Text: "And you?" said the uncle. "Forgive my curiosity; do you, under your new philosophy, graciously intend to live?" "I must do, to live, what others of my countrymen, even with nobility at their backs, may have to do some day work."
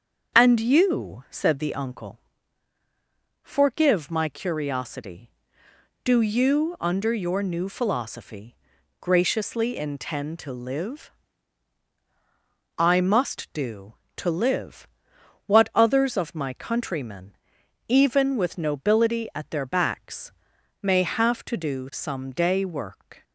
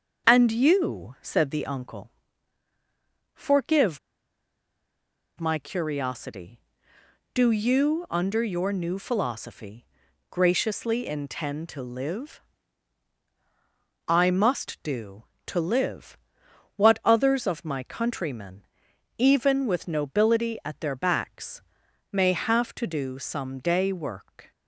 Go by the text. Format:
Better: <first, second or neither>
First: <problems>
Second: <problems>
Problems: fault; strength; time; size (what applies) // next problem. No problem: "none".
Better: first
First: starts louder than the rest; until 1.3 s; 7 dB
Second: starts louder than the rest; until 1.3 s; 6.5 dB // pauses between "Forgive" and "my"; strong; at 3.9 s; 1.3 s long